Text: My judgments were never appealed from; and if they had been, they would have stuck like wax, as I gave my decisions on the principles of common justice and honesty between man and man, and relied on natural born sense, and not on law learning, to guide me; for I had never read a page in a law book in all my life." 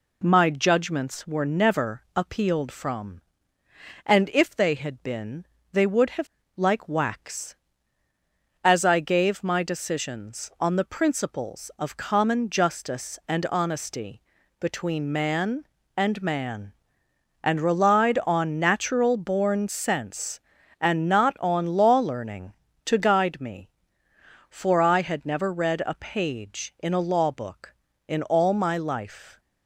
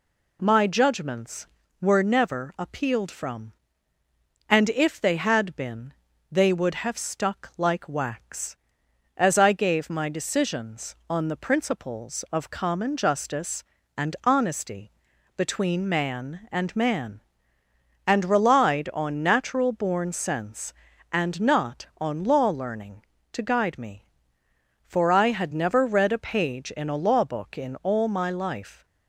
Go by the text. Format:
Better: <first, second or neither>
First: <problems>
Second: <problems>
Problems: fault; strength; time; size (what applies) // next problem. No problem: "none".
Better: second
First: skips "stuck"; at 6.4 s // pauses between "honesty" and "between"; at 14.2 s; 0.38 s long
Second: pauses between "honesty" and "between"; noticeable; at 14.9 s; 0.46 s long